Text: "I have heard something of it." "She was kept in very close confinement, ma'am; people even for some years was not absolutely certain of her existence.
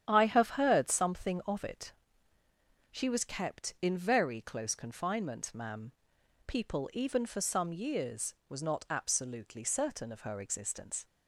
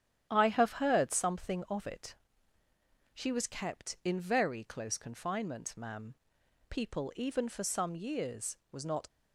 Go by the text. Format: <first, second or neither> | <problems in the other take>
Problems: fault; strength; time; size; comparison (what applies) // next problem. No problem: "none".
first | starts louder than the rest; strong; until 1.3 s; 10.5 dB; strong in the first // stops before "absolutely certain of her existence"; at 9.0 s